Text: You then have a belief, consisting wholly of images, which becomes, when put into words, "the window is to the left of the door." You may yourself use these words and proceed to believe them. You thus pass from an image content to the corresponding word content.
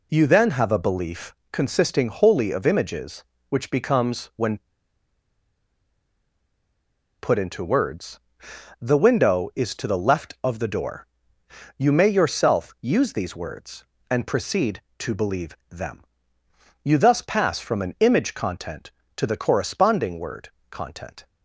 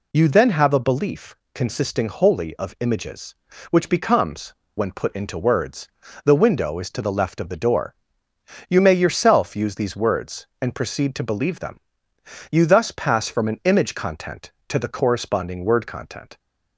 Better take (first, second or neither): second